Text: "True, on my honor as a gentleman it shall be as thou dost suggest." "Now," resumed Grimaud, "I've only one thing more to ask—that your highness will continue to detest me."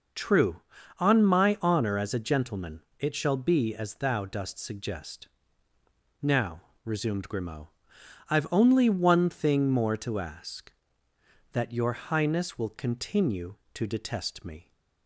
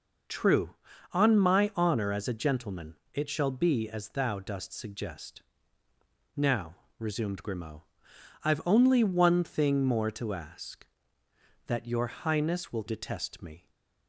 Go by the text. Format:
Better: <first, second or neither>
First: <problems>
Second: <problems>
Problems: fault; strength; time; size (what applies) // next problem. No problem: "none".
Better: first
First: pauses between "gentleman" and "it"; slight; at 2.8 s; 0.16 s long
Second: pauses between "gentleman" and "it"; slight; at 2.9 s; 0.16 s long // skips "continue to"; at 12.8 s